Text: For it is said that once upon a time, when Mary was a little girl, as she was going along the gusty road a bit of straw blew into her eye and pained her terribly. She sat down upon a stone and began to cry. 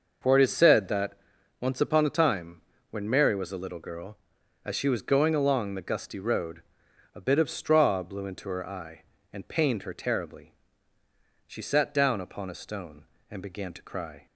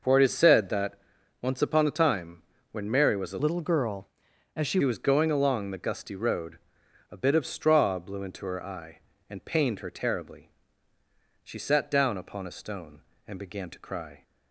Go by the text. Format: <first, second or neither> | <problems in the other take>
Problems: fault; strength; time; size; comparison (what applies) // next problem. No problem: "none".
first | pauses between "that" and "once"; noticeable; at 0.9 s; 0.46 s long; noticeable in the first // changes voice from "little" to "she"; from 3.3 to 4.8 s; 1.5 s long // pauses between "road" and "a"; noticeable; at 6.5 s; 0.54 s long; noticeable in the first